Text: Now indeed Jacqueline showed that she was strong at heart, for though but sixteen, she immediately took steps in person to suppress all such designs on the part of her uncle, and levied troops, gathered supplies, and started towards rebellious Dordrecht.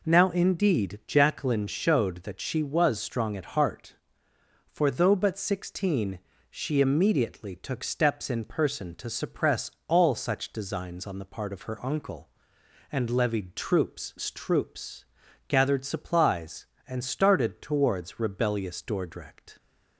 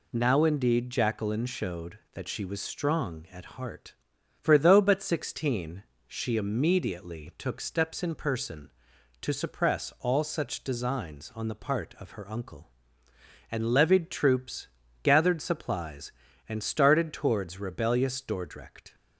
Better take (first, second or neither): second